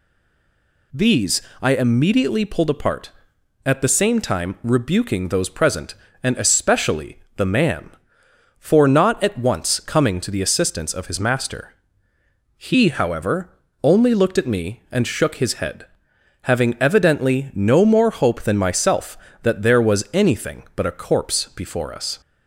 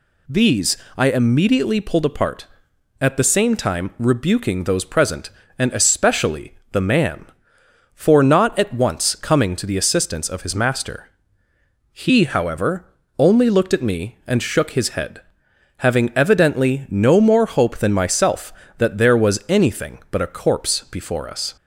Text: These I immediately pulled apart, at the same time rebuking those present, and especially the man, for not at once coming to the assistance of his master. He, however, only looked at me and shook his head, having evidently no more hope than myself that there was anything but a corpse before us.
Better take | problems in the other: second | stays silent before the first word; slight; until 0.9 s; 0.9 s long // pauses between "These" and "I"; slight; at 1.4 s; 0.22 s long; slight in the second // pauses between "especially" and "the"; slight; at 7.1 s; 0.18 s long; slight in the second

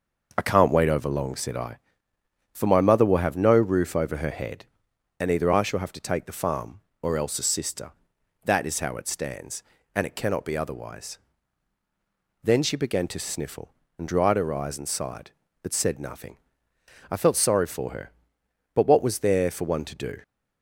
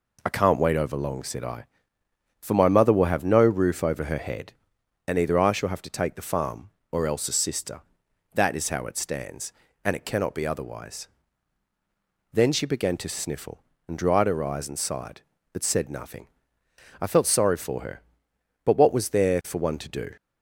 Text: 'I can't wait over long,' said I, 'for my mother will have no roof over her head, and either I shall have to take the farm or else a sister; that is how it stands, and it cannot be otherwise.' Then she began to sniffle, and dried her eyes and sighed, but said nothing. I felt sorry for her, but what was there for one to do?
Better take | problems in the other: second | starts louder than the rest; noticeable; until 1.8 s; 6 dB

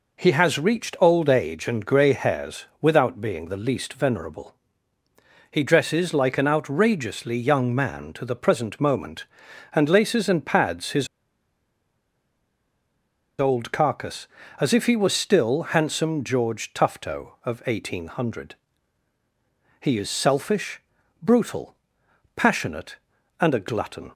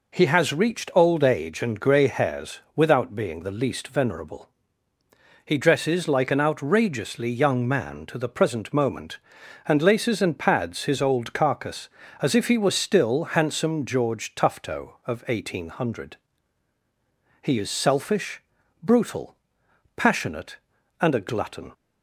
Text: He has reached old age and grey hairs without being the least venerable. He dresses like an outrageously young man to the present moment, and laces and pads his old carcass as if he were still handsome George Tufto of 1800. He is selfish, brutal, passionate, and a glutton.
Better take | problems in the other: second | pauses between "hairs" and "without"; slight; at 2.6 s; 0.16 s long; slight in the second // pauses between "his" and "old"; strong; at 11.0 s; 2.3 s long

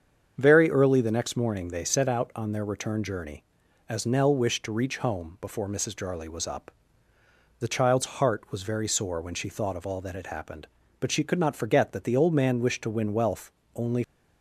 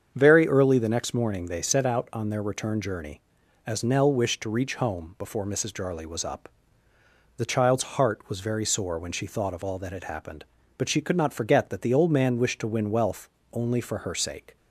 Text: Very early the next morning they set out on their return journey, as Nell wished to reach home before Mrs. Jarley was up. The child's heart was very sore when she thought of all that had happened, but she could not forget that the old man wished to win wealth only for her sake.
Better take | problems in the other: second | starts louder than the rest; strong; until 1.3 s; 7.5 dB; strong in the second // pauses between "wealth" and "only"; slight; at 13.5 s; 0.24 s long; slight in the second // stops before "for her sake"; at 14.0 s

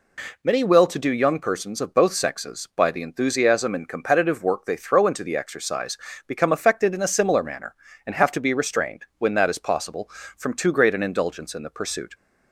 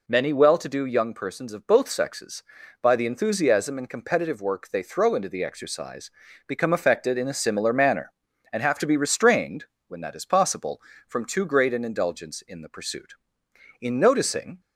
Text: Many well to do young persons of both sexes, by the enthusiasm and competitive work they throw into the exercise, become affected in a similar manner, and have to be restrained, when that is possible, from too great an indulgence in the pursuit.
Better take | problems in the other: first | goes on to say "In noticing"; noticeable; from 13.7 s on; 0.80 s long

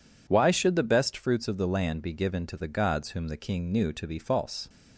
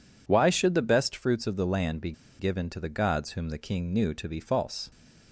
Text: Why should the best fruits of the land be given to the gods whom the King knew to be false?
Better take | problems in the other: first | pauses between "be" and "given"; slight; at 2.1 s; 0.27 s long

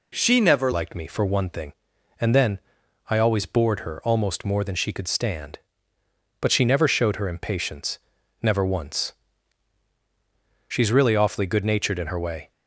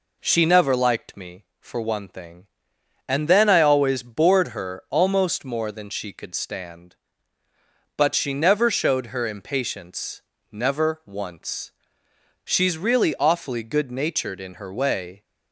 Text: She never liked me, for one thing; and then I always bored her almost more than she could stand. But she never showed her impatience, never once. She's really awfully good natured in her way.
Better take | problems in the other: second | changes voice at "liked"; from 0.7 s on; 11.8 s long // pauses between "then" and "I"; noticeable; at 2.6 s; 0.48 s long

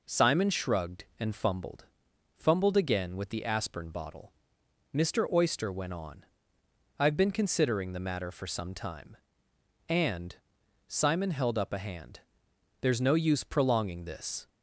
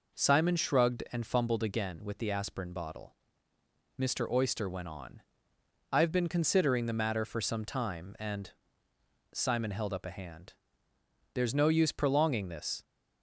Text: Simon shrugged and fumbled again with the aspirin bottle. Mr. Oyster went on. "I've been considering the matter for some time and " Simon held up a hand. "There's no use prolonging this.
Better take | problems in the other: second | says "fumbled" twice; at 2.3 s

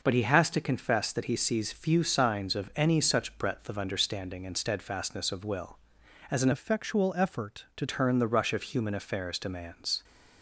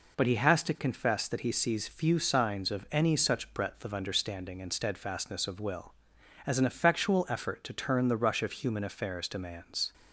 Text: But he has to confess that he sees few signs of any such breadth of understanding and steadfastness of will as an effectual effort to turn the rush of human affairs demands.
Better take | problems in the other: second | changes voice from "effectual" to "to"; from 6.5 to 7.8 s; 1.3 s long

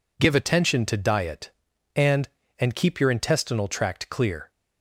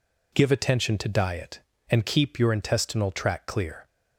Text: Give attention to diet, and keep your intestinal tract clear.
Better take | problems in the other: second | says "and" twice; at 2.5 s

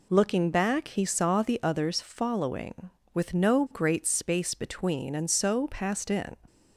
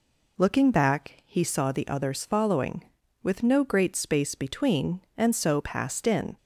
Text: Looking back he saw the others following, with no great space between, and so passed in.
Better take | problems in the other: neither | none

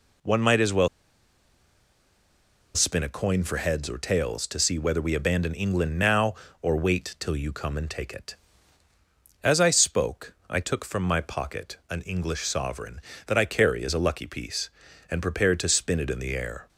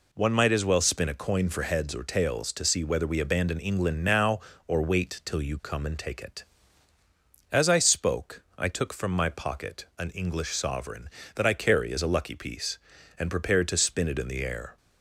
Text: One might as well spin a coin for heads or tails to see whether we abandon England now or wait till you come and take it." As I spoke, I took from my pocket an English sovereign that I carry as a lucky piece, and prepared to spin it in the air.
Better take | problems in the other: second | pauses between "well" and "spin"; strong; at 0.8 s; 1.8 s long

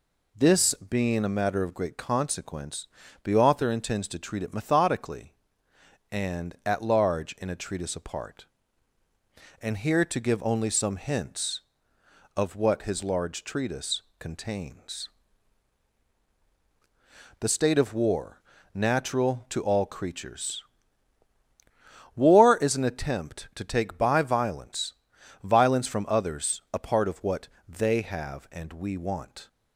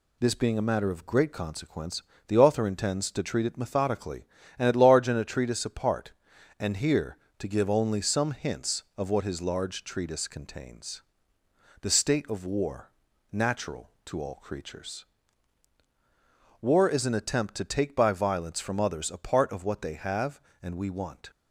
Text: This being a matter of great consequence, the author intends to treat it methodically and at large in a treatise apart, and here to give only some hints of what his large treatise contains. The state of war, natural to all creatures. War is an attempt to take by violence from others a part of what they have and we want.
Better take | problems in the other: second | pauses between "treatise" and "contains"; slight; at 14.0 s; 0.18 s long // says "violence" twice; at 25.4 s // pauses between "what" and "they"; slight; at 27.4 s; 0.20 s long

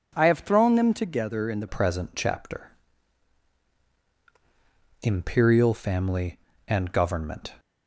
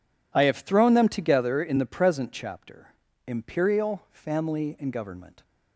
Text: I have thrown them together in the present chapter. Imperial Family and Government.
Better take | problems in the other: second | changes voice at "present"; from 1.6 s on; 5.9 s long

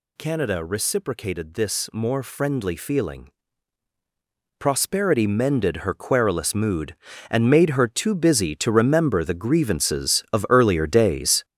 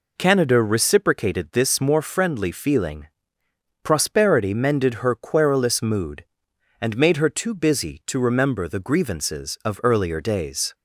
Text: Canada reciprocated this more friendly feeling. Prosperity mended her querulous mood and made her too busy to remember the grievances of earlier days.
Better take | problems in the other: second | gets louder; strong; throughout; 8 dB

